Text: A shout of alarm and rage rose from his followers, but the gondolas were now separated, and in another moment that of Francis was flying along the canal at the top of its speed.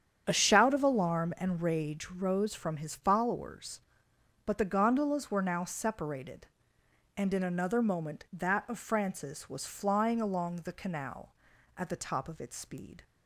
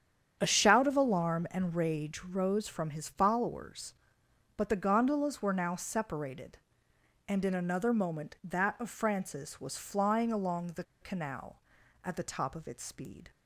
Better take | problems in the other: first | starts louder than the rest; strong; until 1.4 s; 8.5 dB; strong in the first // pauses between "the" and "canal"; slight; at 10.8 s; 0.18 s long

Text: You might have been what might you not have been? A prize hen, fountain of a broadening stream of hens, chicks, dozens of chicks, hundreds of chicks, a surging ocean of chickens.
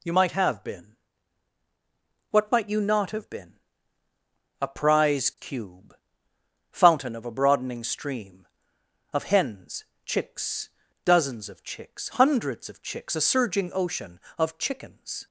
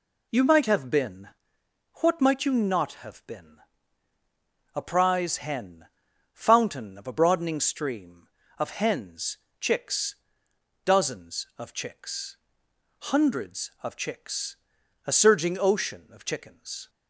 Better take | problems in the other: second | pauses between "been" and "what"; strong; at 0.9 s; 1.3 s long; noticeable in the second // says "cube" for "hen"; at 5.3 s

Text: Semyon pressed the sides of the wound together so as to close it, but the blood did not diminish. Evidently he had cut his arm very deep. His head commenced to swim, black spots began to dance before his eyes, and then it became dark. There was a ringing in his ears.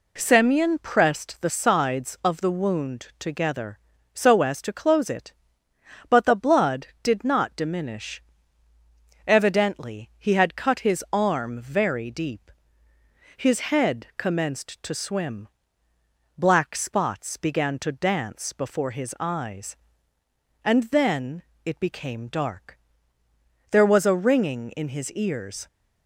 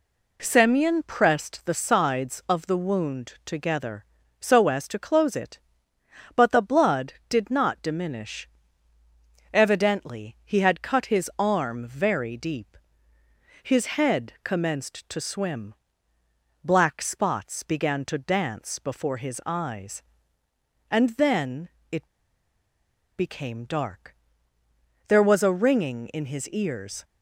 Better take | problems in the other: first | pauses between "then" and "it"; slight; at 21.6 s; 0.22 s long; slight in the first // pauses between "it" and "became"; at 22.0 s; 1.1 s long

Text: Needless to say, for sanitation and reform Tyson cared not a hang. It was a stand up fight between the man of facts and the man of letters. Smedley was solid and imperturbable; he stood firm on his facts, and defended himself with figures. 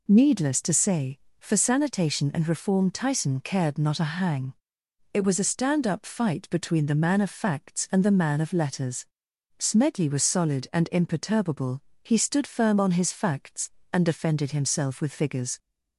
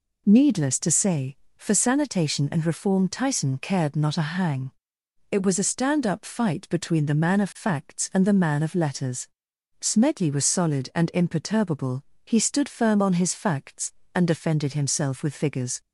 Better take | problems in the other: neither | none

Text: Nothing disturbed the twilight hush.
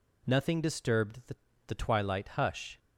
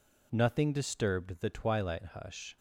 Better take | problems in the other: second | says "the" twice; at 1.6 s

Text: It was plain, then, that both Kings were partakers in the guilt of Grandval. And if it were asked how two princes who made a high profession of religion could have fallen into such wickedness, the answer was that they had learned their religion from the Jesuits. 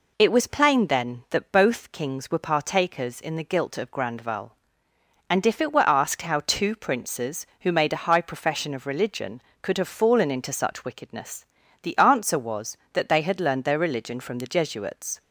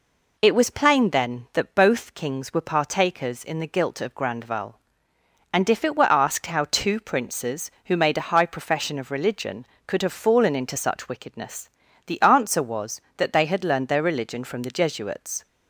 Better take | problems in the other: neither | none

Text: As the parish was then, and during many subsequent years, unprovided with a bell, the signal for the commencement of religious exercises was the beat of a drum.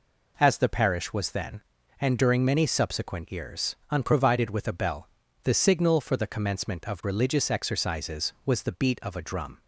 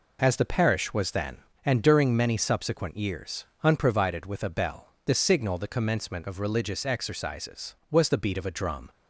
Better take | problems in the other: first | skips "for"; at 5.5 s

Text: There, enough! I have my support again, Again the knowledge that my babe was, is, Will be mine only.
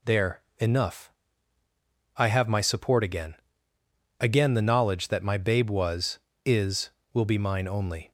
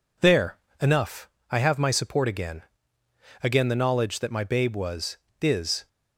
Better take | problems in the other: first | stops before "Will be mine only"; at 5.8 s

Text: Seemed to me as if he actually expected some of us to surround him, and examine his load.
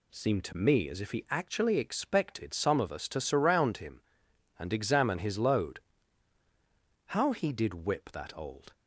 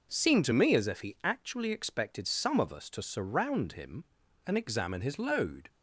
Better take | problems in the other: second | goes on to say "How he did whip that old"; from 7.0 s on; 1.6 s long

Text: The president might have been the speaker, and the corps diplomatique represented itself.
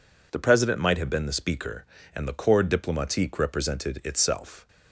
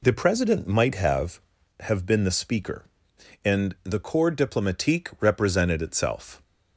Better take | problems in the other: first | says "have" twice; at 1.7 s

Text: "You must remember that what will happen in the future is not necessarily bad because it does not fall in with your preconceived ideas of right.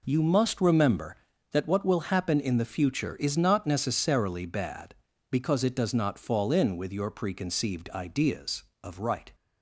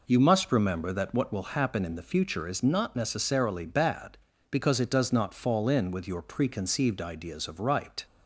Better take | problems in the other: neither | none

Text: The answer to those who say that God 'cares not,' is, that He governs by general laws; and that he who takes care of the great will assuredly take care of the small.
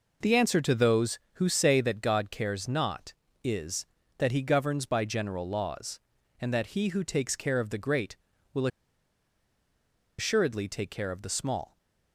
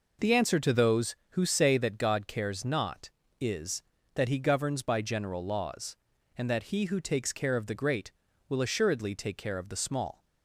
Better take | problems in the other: second | pauses between "will" and "assuredly"; strong; at 8.6 s; 1.5 s long

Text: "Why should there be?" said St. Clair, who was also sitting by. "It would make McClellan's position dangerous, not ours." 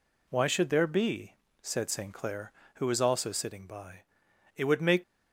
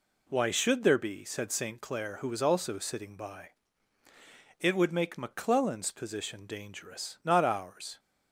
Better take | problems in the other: second | stops before "McClellan's position dangerous not ours"; at 5.0 s

